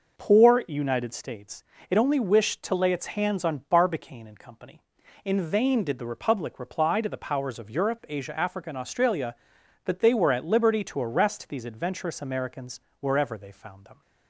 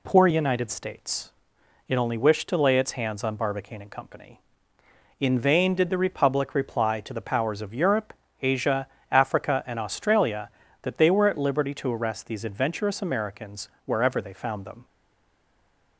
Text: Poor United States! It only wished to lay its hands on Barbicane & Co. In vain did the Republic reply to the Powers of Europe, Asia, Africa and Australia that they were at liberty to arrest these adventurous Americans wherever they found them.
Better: first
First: pauses between "Americans" and "wherever"; slight; at 12.8 s; 0.20 s long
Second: pauses between "Americans" and "wherever"; slight; at 13.7 s; 0.16 s long // stays silent after the last word; from 14.8 s on; 1.1 s long

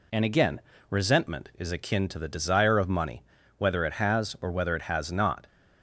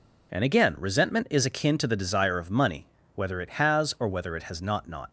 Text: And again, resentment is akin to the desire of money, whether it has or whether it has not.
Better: first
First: none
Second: says "not" twice; at 4.8 s

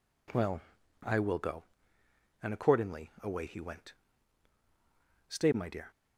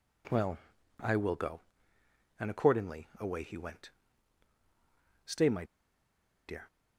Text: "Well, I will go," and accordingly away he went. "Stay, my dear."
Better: first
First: none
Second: pauses between "my" and "dear"; noticeable; at 5.6 s; 0.83 s long

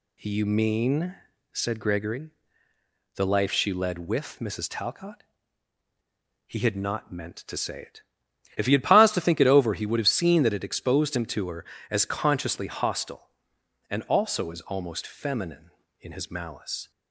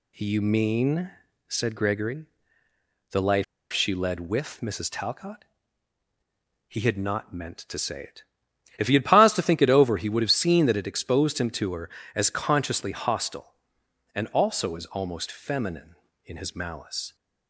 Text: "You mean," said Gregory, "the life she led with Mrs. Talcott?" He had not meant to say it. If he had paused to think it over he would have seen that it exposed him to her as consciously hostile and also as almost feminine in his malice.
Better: first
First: none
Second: pauses between "life" and "she"; slight; at 3.4 s; 0.28 s long

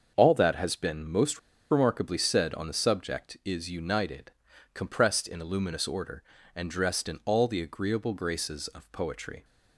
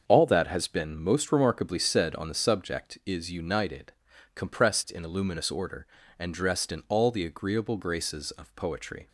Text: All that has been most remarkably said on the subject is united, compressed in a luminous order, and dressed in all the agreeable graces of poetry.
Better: second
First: starts louder than the rest; until 1.1 s; 6.5 dB // pauses between "most" and "remarkably"; slight; at 1.3 s; 0.31 s long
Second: starts louder than the rest; until 1.0 s; 6.5 dB

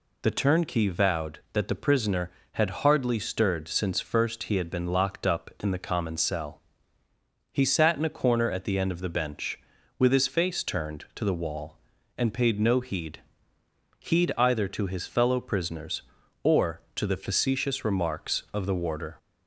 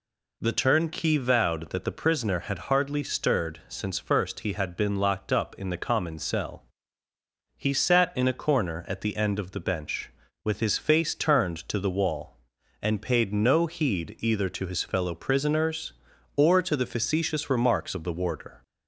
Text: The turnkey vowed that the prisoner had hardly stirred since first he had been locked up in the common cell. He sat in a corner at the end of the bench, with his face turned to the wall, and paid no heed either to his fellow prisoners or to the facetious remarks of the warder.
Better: second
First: says "heed" twice; at 13.9 s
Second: none

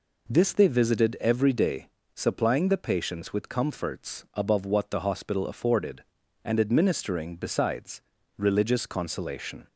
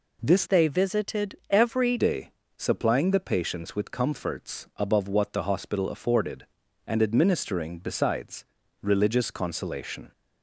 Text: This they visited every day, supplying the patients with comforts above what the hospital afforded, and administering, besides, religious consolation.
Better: first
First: none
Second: changes voice from "they" to "every"; from 0.4 to 1.9 s; 1.5 s long

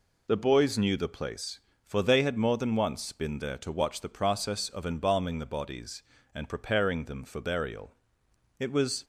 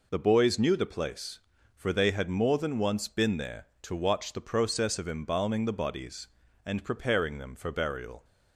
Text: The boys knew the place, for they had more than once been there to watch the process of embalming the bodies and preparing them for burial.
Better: second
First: goes on to say "It was"; slight; from 8.6 s on; 0.44 s long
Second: none

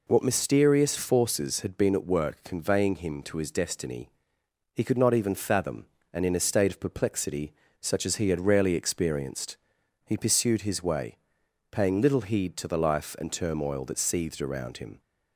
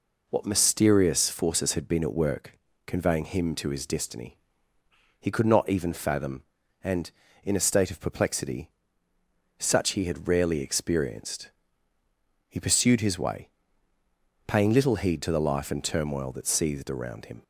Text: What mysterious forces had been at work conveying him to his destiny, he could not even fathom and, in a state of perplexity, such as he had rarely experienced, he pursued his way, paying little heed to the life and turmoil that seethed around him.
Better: first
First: none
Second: pauses between "work" and "conveying"; slight; at 2.5 s; 0.28 s long // skips "as"; at 9.9 s

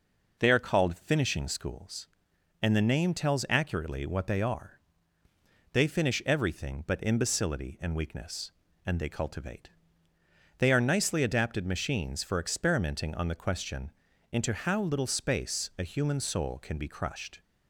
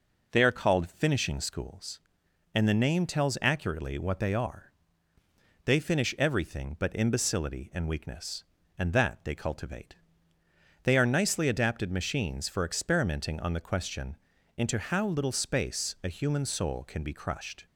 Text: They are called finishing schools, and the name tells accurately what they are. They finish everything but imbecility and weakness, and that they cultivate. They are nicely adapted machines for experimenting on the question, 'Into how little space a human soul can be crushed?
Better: second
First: skips "that"; at 8.9 s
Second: none

